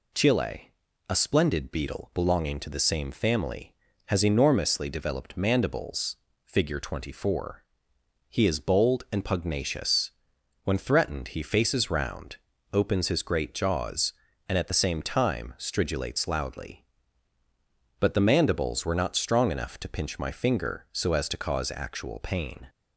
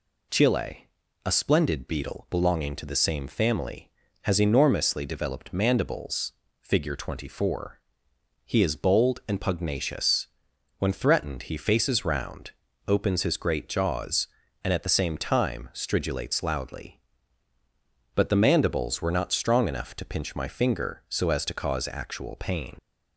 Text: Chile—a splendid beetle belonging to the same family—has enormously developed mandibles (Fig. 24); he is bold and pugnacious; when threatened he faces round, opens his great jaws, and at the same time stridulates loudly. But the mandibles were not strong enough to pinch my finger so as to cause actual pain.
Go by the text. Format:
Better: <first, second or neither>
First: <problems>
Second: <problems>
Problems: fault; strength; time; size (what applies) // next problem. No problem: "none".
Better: first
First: none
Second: leaves "pain" unfinished; at 22.7 s; 70 ms